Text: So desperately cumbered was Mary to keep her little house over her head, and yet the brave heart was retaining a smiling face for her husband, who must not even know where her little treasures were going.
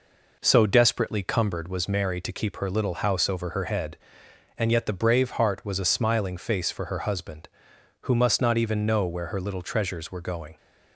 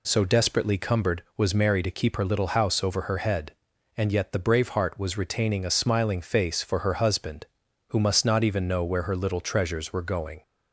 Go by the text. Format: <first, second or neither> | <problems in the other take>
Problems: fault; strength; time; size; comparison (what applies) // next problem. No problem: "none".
second | skips "retaining"; at 5.8 s